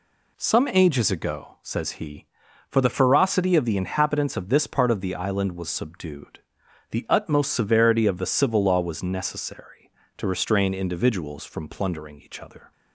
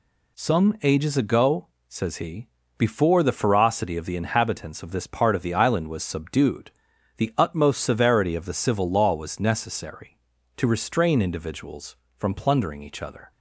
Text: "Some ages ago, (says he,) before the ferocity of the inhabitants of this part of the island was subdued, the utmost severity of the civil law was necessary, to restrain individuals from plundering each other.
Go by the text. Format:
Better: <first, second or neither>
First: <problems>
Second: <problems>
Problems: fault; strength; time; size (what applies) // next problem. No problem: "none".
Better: second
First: says "for" for "before"; at 2.6 s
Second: none